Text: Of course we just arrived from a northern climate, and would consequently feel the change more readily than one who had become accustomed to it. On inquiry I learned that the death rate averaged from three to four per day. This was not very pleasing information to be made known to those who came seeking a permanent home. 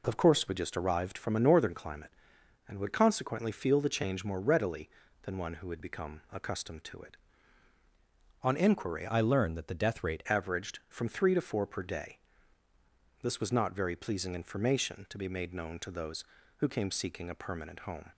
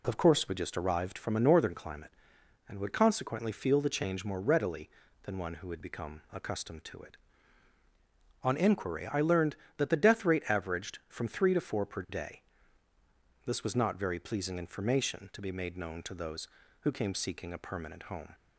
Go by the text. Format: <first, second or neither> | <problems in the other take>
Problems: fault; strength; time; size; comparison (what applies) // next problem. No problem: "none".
second | changes voice from "I" to "rate"; from 9.0 to 10.2 s; 1.2 s long